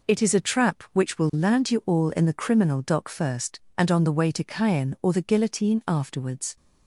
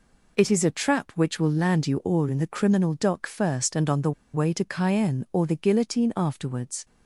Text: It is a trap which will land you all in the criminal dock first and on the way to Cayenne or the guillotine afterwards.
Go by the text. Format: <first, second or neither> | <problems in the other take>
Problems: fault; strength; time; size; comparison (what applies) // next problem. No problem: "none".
first | pauses between "the" and "way"; slight; at 4.1 s; 0.22 s long